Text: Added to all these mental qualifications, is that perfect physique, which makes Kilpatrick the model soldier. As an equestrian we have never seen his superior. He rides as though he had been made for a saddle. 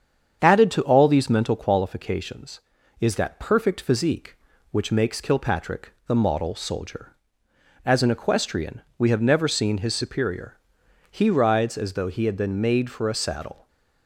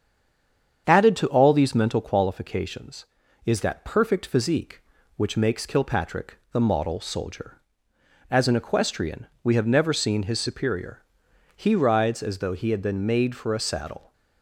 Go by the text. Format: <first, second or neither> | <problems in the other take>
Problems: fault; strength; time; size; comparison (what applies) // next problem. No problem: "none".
first | stays silent before the first word; slight; until 0.8 s; 0.8 s long // starts louder than the rest; strong; until 1.9 s; 8 dB; strong in the first // pauses between "equestrian" and "we"; slight; at 9.2 s; 0.16 s long; slight in the first